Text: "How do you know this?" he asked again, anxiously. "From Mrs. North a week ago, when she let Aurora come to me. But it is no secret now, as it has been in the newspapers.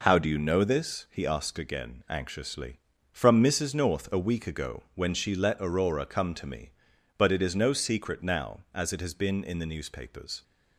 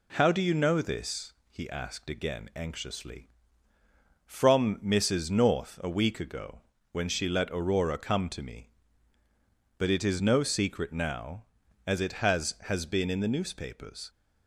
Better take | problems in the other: first | says "has" twice; at 12.6 s

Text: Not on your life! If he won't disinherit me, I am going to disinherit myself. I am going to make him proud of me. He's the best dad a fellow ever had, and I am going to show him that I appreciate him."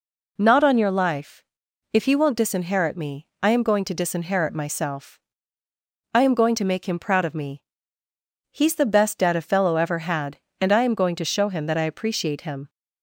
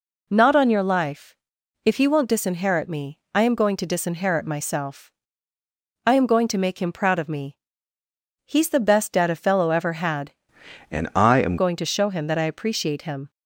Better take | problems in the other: first | changes voice from "and" to "am"; from 10.9 to 11.5 s; 0.6 s long

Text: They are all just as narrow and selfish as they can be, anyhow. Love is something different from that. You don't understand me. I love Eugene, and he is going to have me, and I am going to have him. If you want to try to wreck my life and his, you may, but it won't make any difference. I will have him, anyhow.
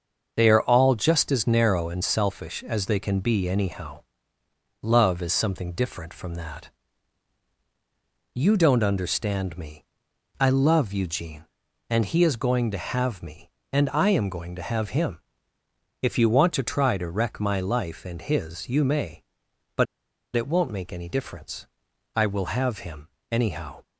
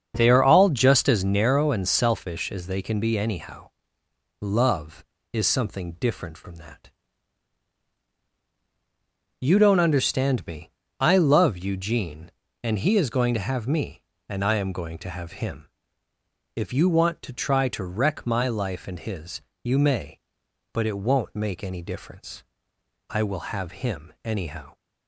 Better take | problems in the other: second | starts louder than the rest; until 1.3 s; 6.5 dB; also in the second // pauses between "but" and "it"; noticeable; at 19.8 s; 0.51 s long

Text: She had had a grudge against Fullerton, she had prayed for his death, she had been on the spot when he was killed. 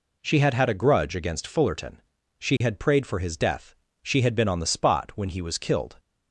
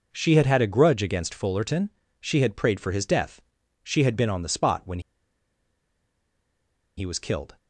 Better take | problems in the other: first | pauses between "when" and "he"; strong; at 4.9 s; 1.9 s long

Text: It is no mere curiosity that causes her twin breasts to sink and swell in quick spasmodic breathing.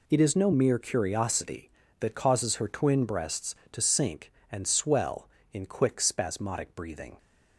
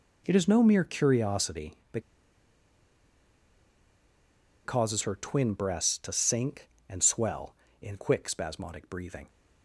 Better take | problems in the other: first | pauses between "that" and "causes"; strong; at 2.0 s; 2.6 s long

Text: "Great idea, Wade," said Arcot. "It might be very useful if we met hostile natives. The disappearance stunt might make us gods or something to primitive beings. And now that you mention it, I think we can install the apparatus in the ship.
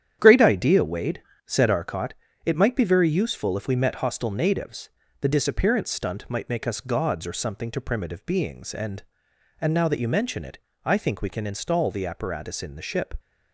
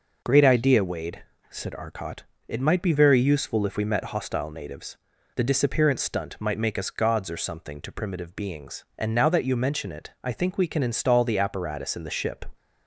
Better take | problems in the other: second | starts louder than the rest; strong; until 1.2 s; 9.5 dB // says "And" twice; at 9.6 s

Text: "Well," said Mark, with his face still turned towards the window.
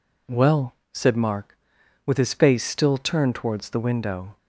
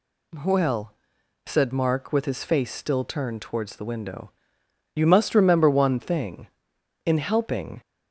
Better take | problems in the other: first | goes on to say "You must remember one thing in helping"; strong; from 4.9 s on; 2.8 s long

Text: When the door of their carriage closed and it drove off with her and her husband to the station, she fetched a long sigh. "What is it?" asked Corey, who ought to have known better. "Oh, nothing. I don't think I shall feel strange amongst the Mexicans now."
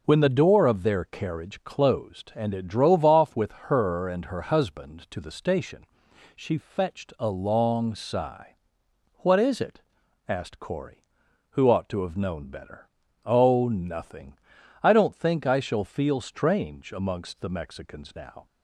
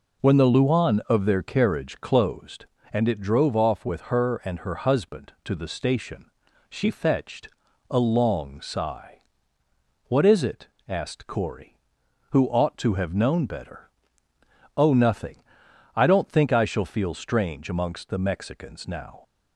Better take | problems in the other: first | says "luan" for "door"; at 0.4 s // pauses between "fetched" and "a"; at 7.4 s; 0.42 s long

